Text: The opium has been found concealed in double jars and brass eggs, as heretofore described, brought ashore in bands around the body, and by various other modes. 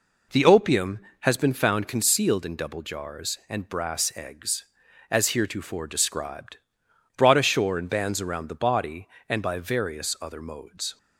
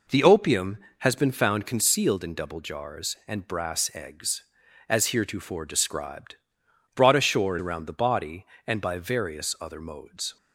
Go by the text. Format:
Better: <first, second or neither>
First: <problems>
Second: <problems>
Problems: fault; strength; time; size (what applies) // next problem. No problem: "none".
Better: first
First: none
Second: skips "in bands"; at 7.5 s